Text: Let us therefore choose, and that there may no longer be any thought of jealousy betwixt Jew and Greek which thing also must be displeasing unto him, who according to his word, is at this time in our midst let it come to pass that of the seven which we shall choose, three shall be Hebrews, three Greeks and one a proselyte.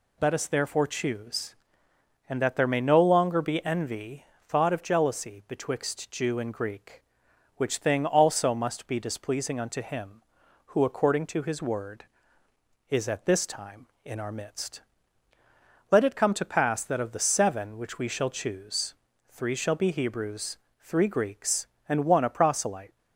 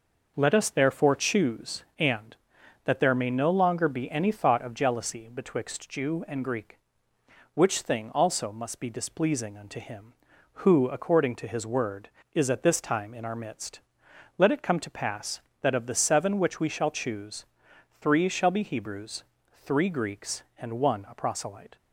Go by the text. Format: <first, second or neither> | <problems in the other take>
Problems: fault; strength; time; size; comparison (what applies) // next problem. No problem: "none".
second | says "envy" for "any"; at 3.6 s // pauses between "midst" and "let"; at 14.8 s; 1.0 s long; noticeable in the second